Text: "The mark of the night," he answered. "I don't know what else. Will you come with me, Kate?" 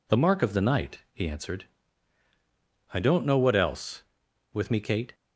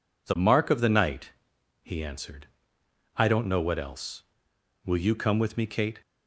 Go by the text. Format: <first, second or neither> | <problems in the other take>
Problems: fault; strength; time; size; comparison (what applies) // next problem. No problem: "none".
second | skips "Will you come"; at 4.2 s